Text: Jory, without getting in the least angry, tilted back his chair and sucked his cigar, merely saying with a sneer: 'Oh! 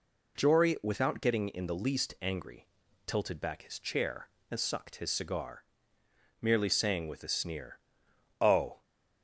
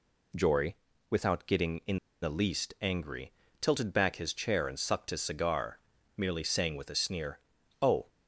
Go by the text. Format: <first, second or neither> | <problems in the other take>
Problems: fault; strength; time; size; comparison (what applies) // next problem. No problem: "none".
first | pauses between "in" and "the"; slight; at 1.9 s; 0.23 s long